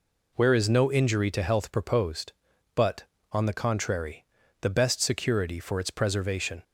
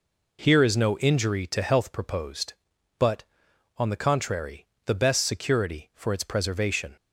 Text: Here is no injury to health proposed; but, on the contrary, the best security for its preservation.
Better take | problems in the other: second | says "Where" for "Here"; at 0.3 s

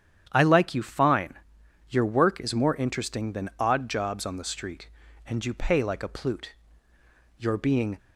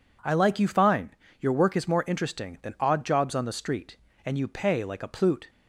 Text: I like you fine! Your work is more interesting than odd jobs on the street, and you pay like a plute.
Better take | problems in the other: second | starts louder than the rest; strong; until 1.3 s; 9.5 dB // goes on to say "You're being"; from 7.3 s on; 0.60 s long

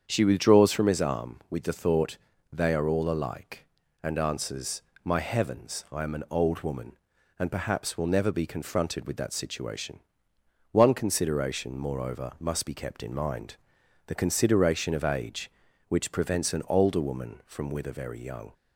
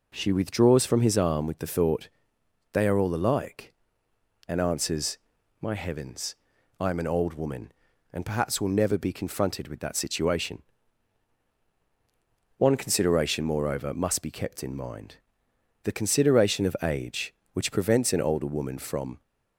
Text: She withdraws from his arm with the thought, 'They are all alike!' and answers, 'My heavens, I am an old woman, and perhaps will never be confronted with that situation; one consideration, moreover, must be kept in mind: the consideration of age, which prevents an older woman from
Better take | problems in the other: second | starts louder than the rest; strong; until 1.0 s; 8 dB // goes on to say "with a very young"; noticeable; from 17.6 s on; 0.84 s long

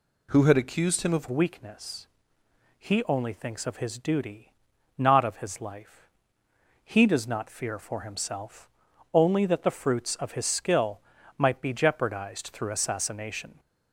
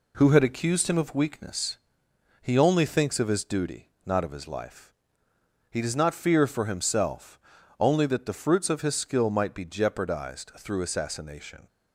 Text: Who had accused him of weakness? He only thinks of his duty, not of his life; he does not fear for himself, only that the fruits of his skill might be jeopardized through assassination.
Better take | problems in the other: second | changes voice at "weakness"; from 1.2 s on; 12.3 s long // pauses between "skill" and "might"; at 10.9 s; 0.38 s long

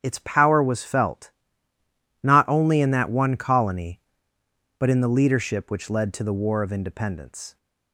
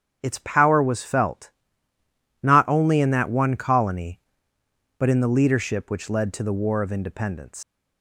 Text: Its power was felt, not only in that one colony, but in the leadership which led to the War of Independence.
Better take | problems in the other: first | starts louder than the rest; strong; until 1.2 s; 8 dB; strong in the first // leaves "Independence" unfinished; at 7.6 s; 135 ms

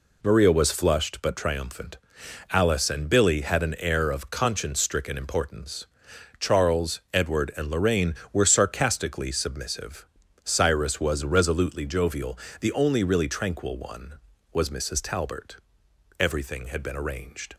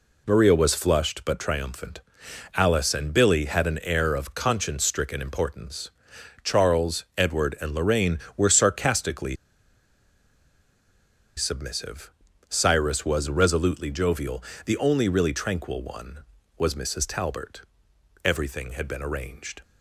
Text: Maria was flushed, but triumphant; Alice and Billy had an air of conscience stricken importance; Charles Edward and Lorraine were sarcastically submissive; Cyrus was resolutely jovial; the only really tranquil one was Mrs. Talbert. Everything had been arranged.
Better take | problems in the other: first | pauses between "sarcastically" and "submissive"; strong; at 9.3 s; 2.0 s long

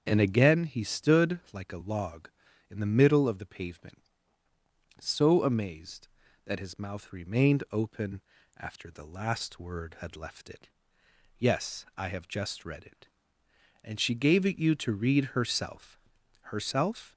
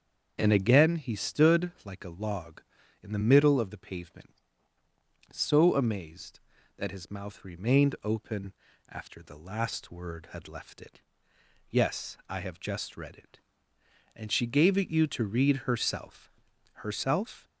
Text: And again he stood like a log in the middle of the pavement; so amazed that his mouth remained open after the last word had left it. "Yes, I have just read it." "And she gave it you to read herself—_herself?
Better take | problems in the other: neither | starts louder than the rest; the same in both // pauses between "open" and "after"; slight; the same in both

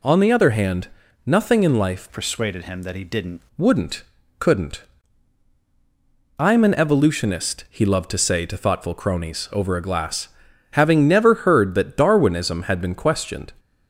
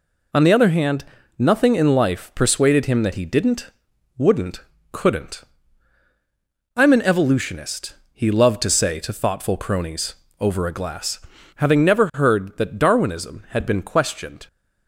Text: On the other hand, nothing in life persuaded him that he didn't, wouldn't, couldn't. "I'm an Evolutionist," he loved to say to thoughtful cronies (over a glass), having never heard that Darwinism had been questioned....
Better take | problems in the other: second | changes voice from "persuaded" to "didn't"; from 2.1 to 3.3 s; 1.2 s long

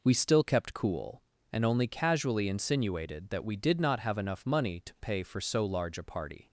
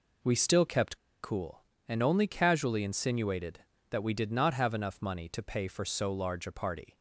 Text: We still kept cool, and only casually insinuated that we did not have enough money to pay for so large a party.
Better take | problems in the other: first | pauses between "kept" and "cool"; slight; at 0.9 s; 0.24 s long

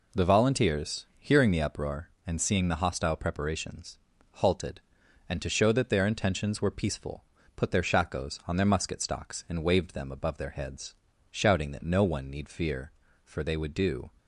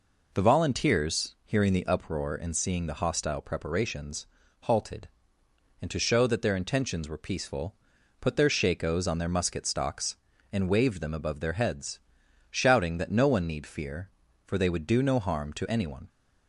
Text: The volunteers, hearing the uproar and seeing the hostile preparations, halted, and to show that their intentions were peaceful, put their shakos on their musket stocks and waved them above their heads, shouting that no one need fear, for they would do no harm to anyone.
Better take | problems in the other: second | stops before "no harm to anyone"; at 14.1 s

